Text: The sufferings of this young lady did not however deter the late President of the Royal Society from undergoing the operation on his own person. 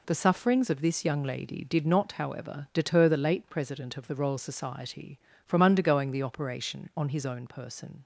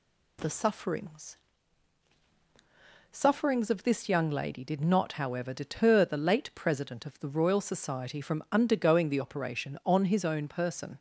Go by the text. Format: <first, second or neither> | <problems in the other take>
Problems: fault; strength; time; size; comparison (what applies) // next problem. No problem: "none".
first | says "sufferings" twice; at 3.1 s